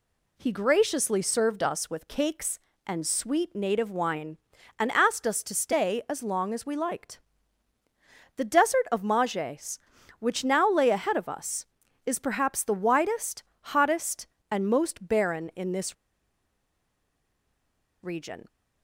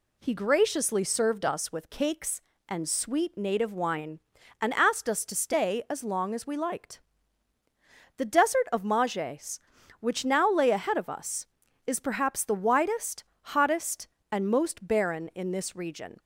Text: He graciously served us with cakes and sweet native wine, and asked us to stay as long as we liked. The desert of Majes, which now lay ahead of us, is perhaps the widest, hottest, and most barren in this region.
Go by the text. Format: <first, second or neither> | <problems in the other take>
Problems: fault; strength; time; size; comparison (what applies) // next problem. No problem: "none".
second | pauses between "this" and "region"; strong; at 15.9 s; 2.0 s long